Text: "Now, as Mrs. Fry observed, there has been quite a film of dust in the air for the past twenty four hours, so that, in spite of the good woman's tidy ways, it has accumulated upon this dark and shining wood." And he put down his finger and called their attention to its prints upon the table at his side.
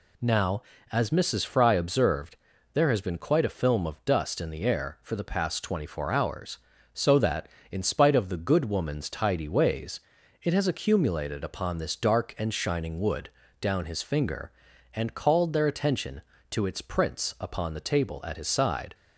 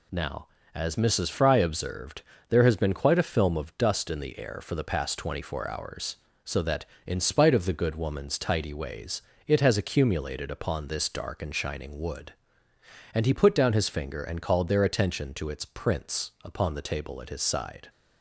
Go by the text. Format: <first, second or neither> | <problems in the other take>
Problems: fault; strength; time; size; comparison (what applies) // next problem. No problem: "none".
second | skips "And he put"; at 13.4 s